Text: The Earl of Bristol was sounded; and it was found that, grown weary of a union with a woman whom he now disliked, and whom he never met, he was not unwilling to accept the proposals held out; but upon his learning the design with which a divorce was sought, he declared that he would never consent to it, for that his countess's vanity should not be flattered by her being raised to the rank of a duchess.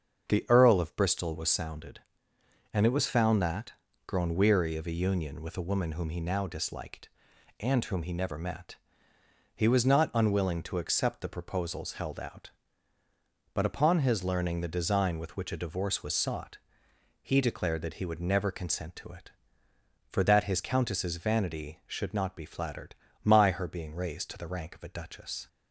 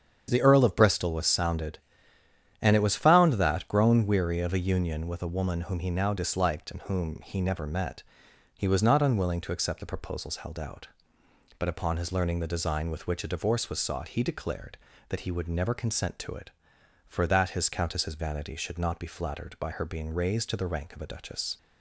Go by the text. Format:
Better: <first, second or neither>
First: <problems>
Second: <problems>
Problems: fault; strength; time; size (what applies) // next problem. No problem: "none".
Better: second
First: starts louder than the rest; until 1.3 s; 7 dB // says "my" for "by"; at 23.2 s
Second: starts louder than the rest; strong; until 1.2 s; 7.5 dB